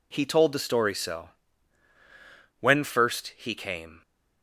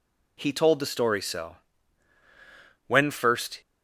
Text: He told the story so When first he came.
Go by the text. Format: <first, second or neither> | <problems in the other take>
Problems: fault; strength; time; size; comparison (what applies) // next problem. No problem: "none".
first | pauses between "so" and "When"; strong; at 1.5 s; 1.3 s long; strong in the first // stops before "he came"; at 3.6 s